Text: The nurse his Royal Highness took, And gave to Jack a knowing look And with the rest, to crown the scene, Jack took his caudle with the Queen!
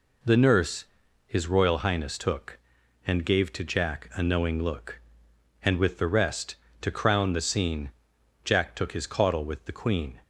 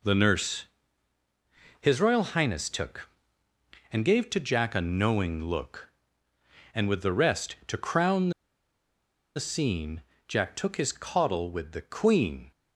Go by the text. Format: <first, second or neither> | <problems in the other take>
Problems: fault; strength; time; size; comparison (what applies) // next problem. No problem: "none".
first | pauses between "nurse" and "his"; at 0.6 s; 1.1 s long; also in the first // pauses between "crown" and "the"; at 8.2 s; 1.0 s long